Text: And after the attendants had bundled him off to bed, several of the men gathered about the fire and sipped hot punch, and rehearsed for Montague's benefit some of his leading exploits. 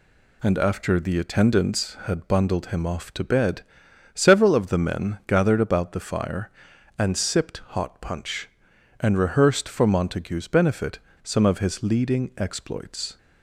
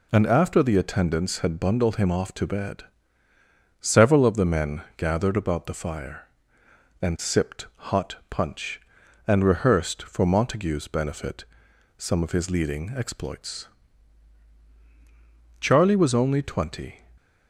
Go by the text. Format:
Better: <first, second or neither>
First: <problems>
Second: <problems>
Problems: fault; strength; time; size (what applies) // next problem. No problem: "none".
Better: first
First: pauses between "benefit" and "some"; slight; at 10.9 s; 0.23 s long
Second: pauses between "benefit" and "some"; noticeable; at 11.4 s; 0.52 s long // goes on to say "Charlie was only twenty"; from 15.6 s on; 1.4 s long